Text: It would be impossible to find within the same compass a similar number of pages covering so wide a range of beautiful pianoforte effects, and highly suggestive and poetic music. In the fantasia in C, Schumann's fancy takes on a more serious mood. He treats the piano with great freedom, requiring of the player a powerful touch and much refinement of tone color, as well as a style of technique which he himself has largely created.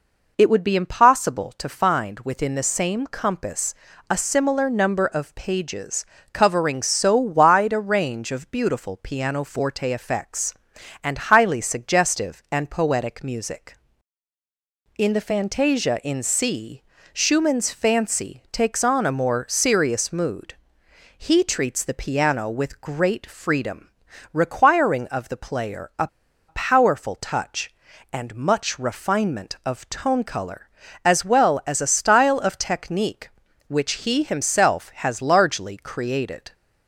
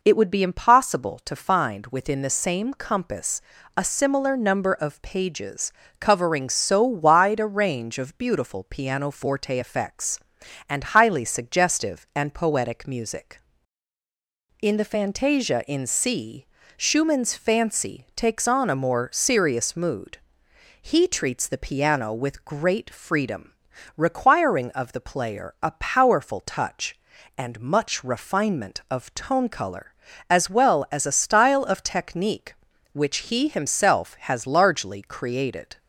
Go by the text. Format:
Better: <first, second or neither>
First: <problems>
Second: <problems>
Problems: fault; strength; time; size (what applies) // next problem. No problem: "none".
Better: second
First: pauses between "compass" and "a"; at 3.7 s; 0.38 s long // pauses between "pages" and "covering"; slight; at 6.0 s; 0.28 s long // pauses between "a" and "powerful"; at 26.0 s; 0.39 s long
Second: pauses between "compass" and "a"; at 3.3 s; 0.38 s long // pauses between "pages" and "covering"; slight; at 5.7 s; 0.28 s long